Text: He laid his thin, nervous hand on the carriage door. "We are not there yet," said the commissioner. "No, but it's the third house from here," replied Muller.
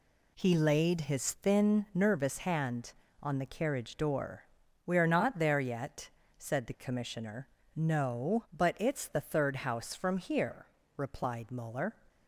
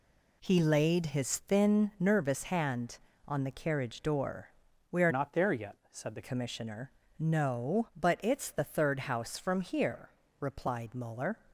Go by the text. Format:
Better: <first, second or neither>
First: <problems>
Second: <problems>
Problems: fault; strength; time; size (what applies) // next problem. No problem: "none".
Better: first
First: none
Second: changes voice from "not" to "the"; from 5.1 to 6.2 s; 1.1 s long